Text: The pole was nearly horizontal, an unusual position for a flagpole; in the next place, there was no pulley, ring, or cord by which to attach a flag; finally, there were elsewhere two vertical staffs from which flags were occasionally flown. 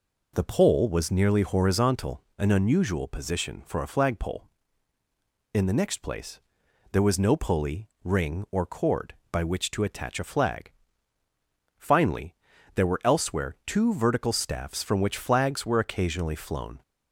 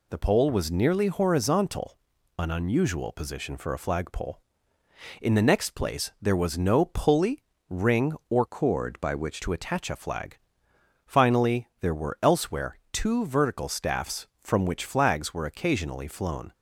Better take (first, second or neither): first